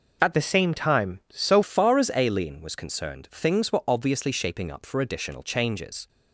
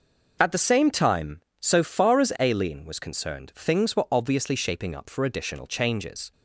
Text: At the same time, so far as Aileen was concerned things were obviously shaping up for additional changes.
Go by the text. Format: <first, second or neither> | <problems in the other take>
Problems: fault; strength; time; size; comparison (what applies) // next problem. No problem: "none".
second | changes voice from "the" to "so"; from 0.3 to 1.6 s; 1.3 s long